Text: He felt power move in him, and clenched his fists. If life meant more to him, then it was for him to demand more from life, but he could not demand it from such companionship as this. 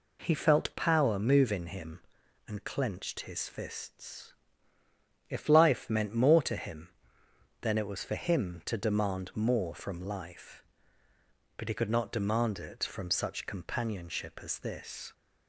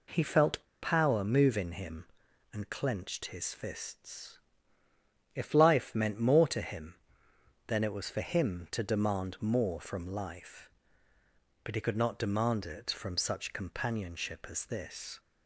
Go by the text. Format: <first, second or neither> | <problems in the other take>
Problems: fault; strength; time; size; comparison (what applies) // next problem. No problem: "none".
first | pauses between "felt" and "power"; slight; at 0.6 s; 0.19 s long